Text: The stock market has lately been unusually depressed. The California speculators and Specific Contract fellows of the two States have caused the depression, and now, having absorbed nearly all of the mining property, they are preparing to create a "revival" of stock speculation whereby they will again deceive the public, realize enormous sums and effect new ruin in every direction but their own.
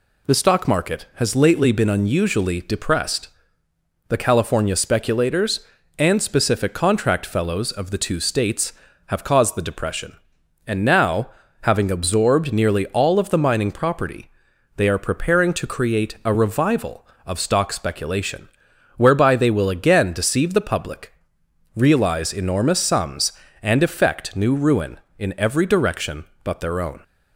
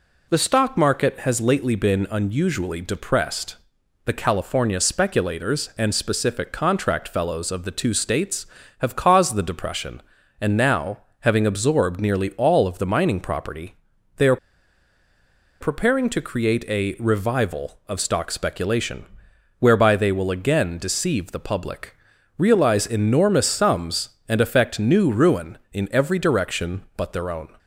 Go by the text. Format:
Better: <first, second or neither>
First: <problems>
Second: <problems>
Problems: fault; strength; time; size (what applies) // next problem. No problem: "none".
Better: first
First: pauses between "speculation" and "whereby"; noticeable; at 18.4 s; 0.50 s long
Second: pauses between "are" and "preparing"; at 14.3 s; 1.2 s long // pauses between "speculation" and "whereby"; noticeable; at 19.0 s; 0.54 s long